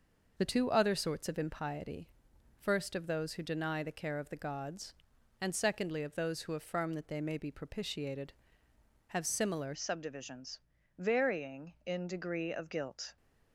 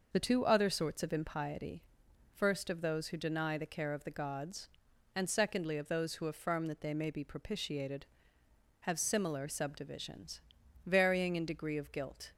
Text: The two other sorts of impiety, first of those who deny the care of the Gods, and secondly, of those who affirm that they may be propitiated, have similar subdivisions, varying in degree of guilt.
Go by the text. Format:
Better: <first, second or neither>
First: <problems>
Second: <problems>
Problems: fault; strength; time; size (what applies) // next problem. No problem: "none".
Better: second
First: changes voice at "subdivisions"; from 9.7 s on; 3.4 s long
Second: none